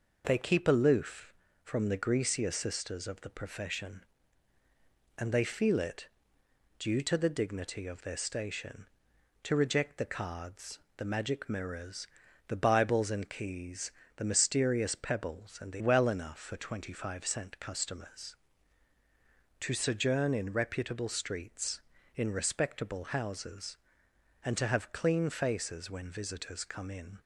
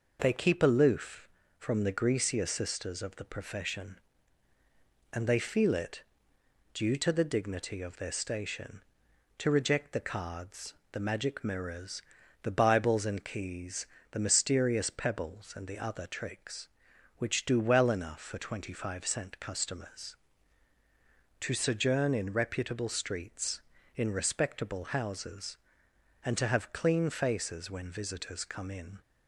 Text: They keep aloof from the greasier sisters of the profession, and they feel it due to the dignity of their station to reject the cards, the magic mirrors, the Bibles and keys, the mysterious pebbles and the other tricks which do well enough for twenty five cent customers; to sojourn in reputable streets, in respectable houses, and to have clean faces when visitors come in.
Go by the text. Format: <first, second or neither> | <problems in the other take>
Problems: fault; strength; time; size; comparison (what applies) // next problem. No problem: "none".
second | pauses between "it" and "due"; noticeable; at 6.0 s; 0.72 s long; noticeable in the second // skips "other tricks which do"; at 15.8 s